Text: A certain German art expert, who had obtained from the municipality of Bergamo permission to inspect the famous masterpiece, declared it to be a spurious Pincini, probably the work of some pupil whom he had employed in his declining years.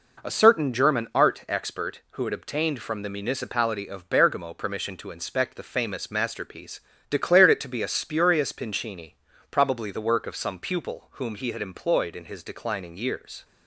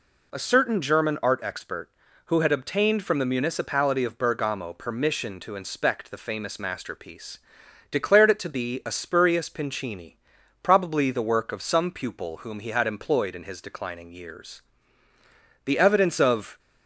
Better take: first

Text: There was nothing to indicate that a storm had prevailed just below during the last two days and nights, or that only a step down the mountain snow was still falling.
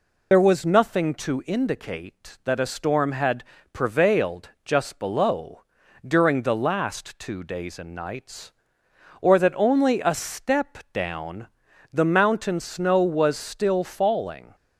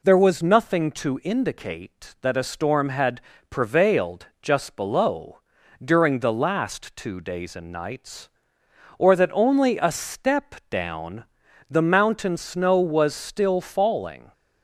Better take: second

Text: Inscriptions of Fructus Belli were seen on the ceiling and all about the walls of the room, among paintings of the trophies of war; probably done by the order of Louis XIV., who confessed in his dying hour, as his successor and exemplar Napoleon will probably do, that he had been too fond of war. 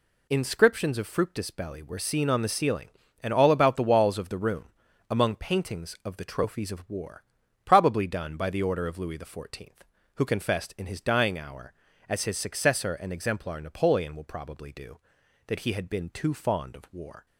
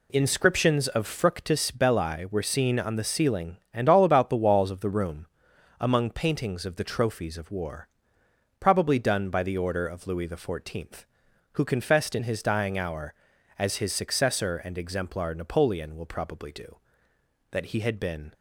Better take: first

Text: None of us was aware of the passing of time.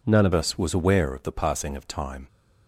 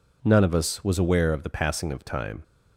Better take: second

